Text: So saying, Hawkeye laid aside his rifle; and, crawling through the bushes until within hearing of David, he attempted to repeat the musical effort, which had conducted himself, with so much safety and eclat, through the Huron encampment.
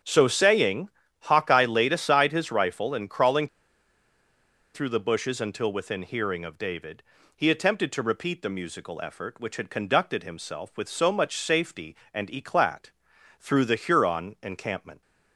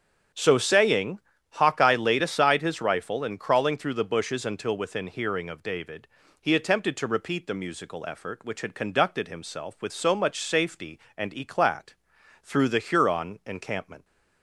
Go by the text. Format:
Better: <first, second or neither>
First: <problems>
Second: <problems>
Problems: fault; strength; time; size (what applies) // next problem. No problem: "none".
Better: second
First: starts louder than the rest; strong; until 1.3 s; 7.5 dB // pauses between "crawling" and "through"; strong; at 3.4 s; 1.2 s long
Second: starts louder than the rest; strong; until 1.6 s; 7.5 dB